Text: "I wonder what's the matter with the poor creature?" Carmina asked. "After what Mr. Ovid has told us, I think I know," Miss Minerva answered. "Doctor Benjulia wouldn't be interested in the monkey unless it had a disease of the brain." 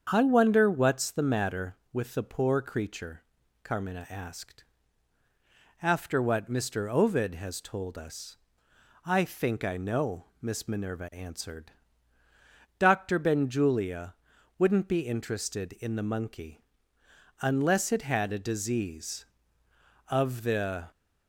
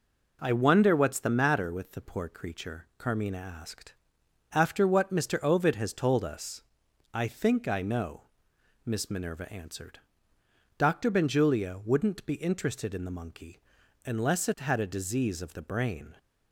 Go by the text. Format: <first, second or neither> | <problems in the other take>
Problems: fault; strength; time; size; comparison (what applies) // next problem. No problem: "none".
second | starts louder than the rest; strong; until 1.1 s; 7 dB // pauses between "Benjulia" and "wouldn't"; at 14.1 s; 0.44 s long // pauses between "monkey" and "unless"; noticeable; at 16.5 s; 0.80 s long; noticeable in the second // stops before "brain"; at 20.9 s